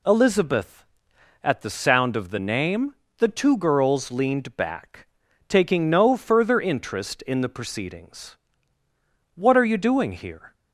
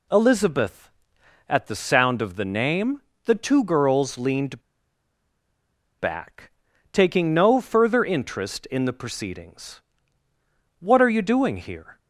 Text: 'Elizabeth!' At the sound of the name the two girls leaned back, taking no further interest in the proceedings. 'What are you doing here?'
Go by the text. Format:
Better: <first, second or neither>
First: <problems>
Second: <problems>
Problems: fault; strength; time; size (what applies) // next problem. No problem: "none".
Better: first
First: pauses between "name" and "the"; slight; at 2.9 s; 0.24 s long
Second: pauses between "name" and "the"; slight; at 3.0 s; 0.24 s long // pauses between "leaned" and "back"; strong; at 4.6 s; 1.3 s long